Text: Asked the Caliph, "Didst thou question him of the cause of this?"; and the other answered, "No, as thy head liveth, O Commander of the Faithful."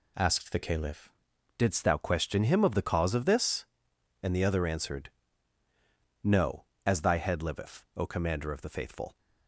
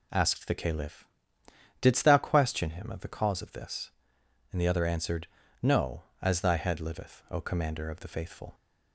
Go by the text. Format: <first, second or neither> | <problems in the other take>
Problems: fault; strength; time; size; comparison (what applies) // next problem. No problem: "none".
second | changes voice at "Didst"; from 1.5 s on; 7.6 s long